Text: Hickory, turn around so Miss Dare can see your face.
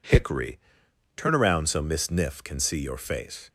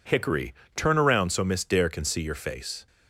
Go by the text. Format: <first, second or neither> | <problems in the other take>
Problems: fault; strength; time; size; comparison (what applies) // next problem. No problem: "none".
second | says "Niff" for "Dare"; at 2.0 s